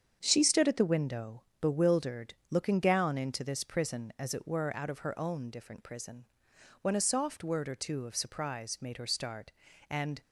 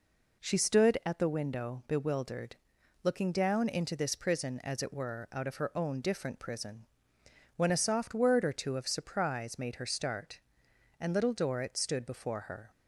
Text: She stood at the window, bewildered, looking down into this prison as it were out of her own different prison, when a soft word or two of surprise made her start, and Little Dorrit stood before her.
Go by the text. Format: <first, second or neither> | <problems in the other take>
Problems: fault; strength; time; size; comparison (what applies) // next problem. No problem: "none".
second | starts louder than the rest; strong; until 1.2 s; 7.5 dB // stops before "Little Dorrit stood before her"; at 10.2 s